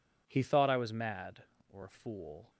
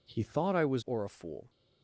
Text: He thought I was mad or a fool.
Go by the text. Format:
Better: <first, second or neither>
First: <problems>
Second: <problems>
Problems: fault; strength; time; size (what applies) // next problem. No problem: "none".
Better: first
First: none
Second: skips "mad"; at 0.8 s